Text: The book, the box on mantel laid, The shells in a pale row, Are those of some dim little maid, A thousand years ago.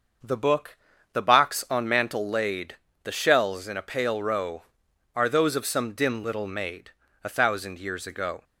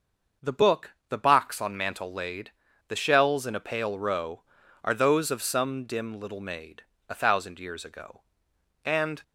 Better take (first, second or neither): first